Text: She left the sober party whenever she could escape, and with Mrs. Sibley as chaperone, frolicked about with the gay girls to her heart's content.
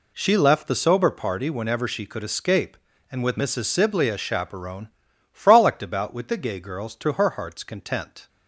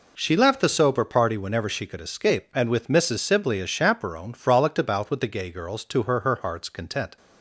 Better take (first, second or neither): first